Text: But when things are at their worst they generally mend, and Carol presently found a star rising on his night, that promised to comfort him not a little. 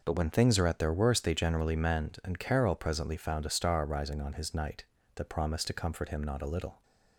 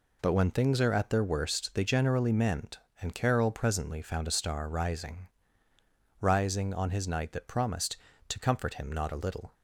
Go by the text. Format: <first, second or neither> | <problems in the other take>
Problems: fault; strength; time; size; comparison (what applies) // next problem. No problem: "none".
first | says "rising" twice; at 6.2 s